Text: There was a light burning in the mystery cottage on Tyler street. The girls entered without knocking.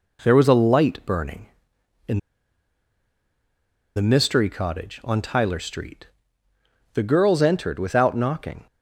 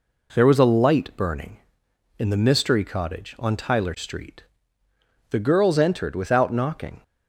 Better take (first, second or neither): second